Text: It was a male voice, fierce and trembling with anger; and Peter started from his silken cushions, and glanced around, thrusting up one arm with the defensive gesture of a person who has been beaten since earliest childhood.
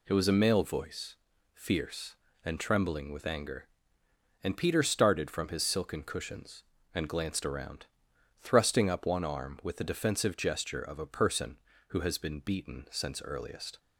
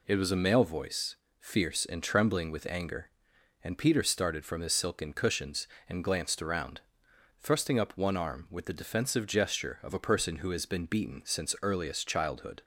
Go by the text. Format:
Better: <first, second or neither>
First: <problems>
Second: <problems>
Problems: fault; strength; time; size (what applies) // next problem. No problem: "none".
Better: second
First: stops before "childhood"; at 13.7 s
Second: none